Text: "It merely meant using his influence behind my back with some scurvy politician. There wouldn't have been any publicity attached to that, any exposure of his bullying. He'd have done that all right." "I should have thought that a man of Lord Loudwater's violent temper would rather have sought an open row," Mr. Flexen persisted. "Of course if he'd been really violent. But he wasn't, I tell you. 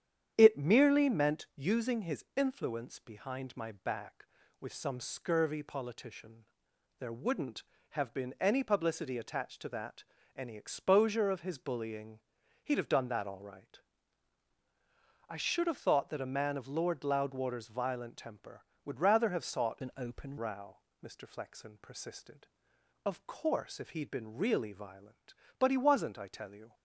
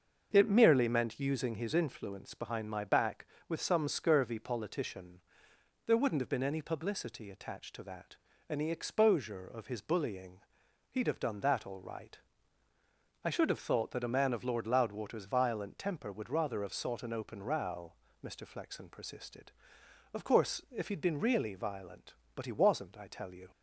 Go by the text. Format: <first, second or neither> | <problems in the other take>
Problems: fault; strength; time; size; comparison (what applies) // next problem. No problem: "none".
second | starts louder than the rest; strong; until 1.3 s; 9 dB; also in the second // changes voice from "an" to "open"; from 19.8 to 20.3 s; 0.5 s long